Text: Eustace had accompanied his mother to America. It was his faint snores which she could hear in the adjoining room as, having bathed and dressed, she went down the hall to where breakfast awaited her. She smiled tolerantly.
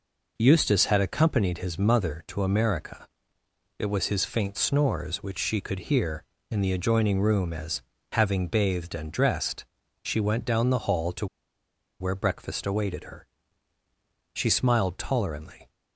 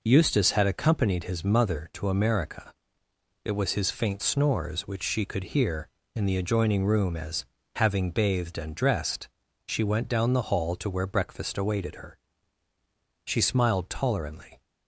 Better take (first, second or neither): second